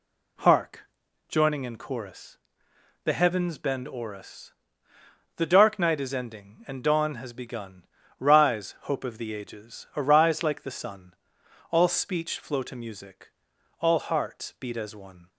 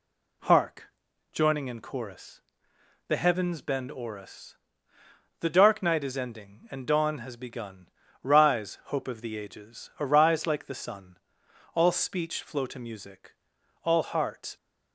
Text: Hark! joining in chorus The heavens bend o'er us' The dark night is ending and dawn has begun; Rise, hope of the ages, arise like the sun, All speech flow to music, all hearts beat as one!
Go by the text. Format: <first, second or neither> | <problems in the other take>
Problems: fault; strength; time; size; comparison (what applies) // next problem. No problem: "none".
first | pauses between "chorus" and "The"; noticeable; at 2.3 s; 0.66 s long; noticeable in the first // pauses between "us" and "The"; noticeable; at 4.5 s; 0.84 s long; noticeable in the first // stops before "beat as one"; at 14.5 s